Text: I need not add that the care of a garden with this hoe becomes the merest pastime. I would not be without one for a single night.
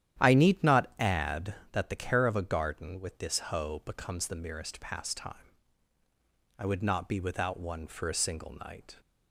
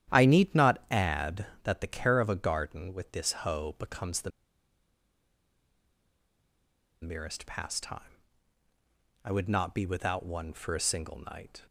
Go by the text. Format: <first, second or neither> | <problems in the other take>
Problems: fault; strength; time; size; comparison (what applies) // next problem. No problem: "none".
first | starts louder than the rest; strong; until 1.1 s; 11 dB; strong in the first // pauses between "the" and "merest"; strong; at 4.3 s; 2.7 s long